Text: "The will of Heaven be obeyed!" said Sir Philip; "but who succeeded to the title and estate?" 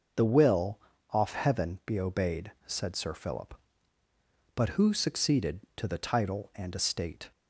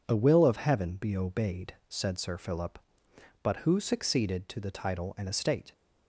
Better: second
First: starts louder than the rest; noticeable; until 1.4 s; 6 dB // says "off" for "of"; at 1.1 s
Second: none

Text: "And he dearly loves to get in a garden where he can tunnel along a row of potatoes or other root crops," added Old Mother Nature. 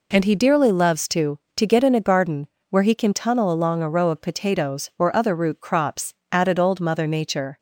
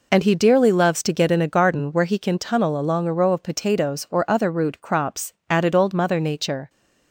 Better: second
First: says "to" twice; at 1.5 s // pauses between "garden" and "where"; slight; at 2.4 s; 0.22 s long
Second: none

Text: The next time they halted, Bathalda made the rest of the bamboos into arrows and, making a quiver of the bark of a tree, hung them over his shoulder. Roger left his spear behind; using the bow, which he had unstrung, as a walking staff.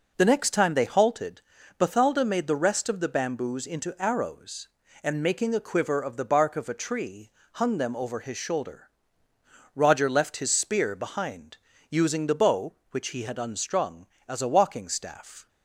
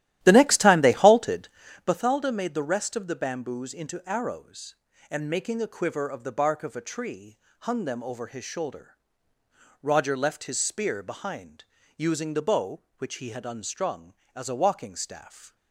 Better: first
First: none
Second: starts louder than the rest; strong; until 2.0 s; 13.5 dB

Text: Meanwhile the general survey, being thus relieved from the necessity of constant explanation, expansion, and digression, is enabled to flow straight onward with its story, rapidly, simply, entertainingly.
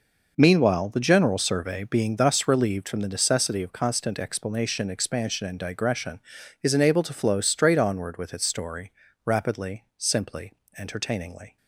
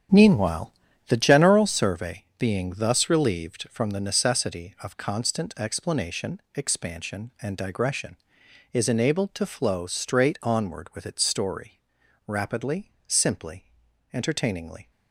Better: first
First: none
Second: starts louder than the rest; strong; until 1.7 s; 8.5 dB // pauses between "Meanwhile" and "the"; slight; at 0.7 s; 0.34 s long

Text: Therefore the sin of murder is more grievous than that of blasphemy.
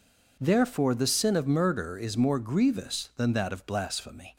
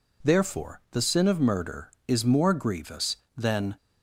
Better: first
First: none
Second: stops before "that of blasphemy"; at 3.7 s

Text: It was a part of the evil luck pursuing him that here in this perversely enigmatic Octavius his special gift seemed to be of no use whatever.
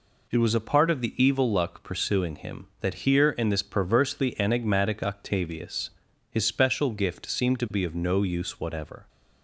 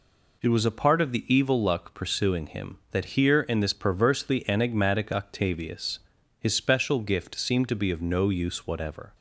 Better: neither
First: pauses between "Octavius" and "his"; at 5.8 s; 0.40 s long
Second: pauses between "Octavius" and "his"; at 5.9 s; 0.40 s long

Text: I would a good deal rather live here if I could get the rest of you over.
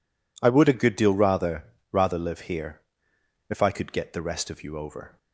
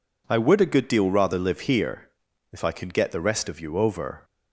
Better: second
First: says "rather" twice; at 1.9 s // pauses between "here" and "if"; noticeable; at 2.8 s; 0.68 s long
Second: pauses between "here" and "if"; at 2.0 s; 0.42 s long

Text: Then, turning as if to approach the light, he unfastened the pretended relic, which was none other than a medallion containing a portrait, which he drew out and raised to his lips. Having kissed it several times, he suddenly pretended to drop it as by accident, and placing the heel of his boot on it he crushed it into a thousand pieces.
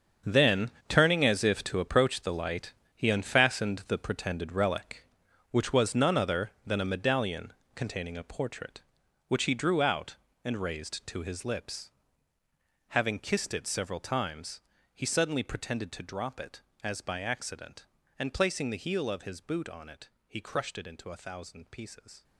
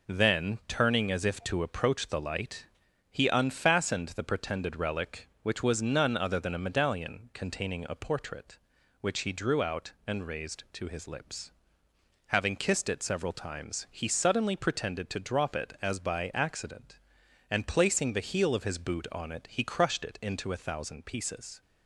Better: second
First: gets quieter; strong; throughout; 13 dB // pauses between "medallion" and "containing"; slight; at 7.5 s; 0.24 s long // pauses between "it" and "he"; slight; at 20.0 s; 0.20 s long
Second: none

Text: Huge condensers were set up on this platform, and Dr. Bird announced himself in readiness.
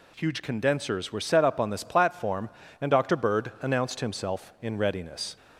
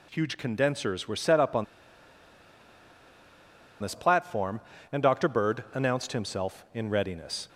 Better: first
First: none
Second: pauses between "on" and "this"; strong; at 1.6 s; 2.1 s long

